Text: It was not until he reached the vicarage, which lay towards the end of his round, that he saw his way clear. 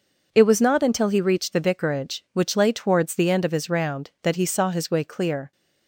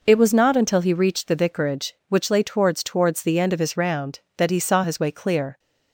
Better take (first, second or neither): first